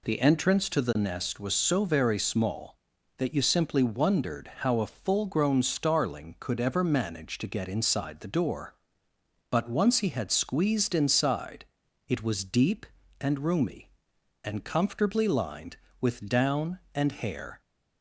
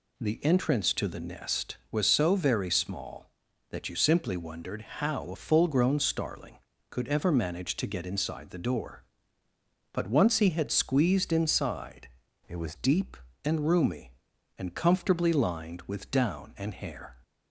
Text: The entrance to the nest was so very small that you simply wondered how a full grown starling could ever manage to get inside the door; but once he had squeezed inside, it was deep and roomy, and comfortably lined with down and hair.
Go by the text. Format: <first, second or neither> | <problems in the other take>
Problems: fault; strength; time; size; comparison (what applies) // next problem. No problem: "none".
first | pauses between "wondered" and "how"; slight; at 4.8 s; 0.18 s long // changes voice from "it" to "was"; from 12.4 to 12.7 s; 0.3 s long